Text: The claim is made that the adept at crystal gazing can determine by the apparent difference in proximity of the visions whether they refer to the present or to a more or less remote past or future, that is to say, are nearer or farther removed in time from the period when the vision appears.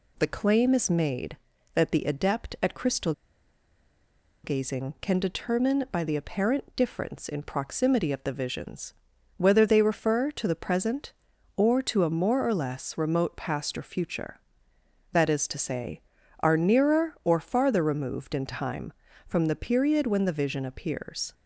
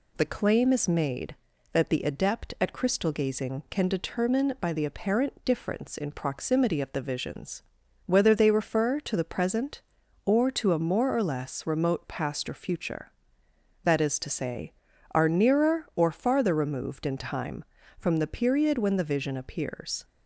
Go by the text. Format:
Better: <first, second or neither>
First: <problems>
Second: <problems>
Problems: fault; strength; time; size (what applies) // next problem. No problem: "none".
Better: second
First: pauses between "crystal" and "gazing"; strong; at 3.1 s; 1.3 s long // pauses between "visions" and "whether"; at 8.9 s; 0.44 s long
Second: pauses between "visions" and "whether"; at 7.6 s; 0.44 s long